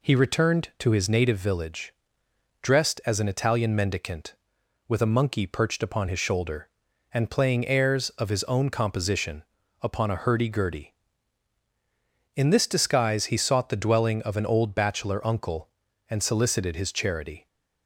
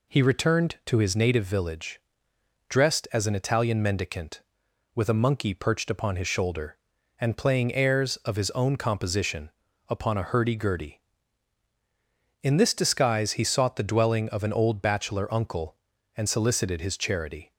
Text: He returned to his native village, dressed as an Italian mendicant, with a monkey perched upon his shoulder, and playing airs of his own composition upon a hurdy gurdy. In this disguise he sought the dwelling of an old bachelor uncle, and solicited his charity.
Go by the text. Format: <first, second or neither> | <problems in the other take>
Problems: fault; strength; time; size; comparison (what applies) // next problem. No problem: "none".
neither | pauses between "composition" and "upon"; the same in both